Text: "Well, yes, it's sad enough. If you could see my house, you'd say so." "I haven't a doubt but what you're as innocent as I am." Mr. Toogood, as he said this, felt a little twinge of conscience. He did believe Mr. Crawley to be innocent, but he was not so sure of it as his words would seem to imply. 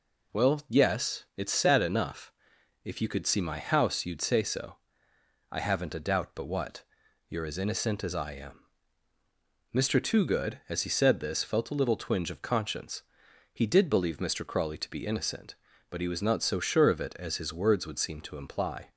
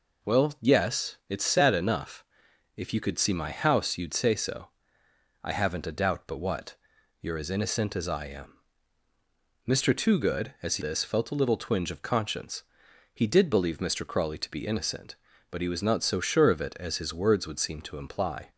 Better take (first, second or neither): first